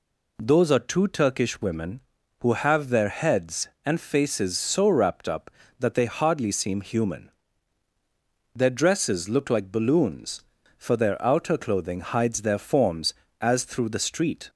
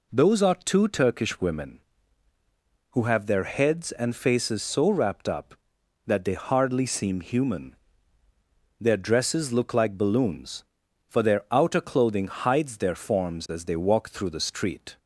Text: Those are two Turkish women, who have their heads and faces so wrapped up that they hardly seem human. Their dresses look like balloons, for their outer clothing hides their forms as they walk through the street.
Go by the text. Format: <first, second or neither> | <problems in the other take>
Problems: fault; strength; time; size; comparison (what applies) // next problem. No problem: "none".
second | skips "they walk"; at 13.6 s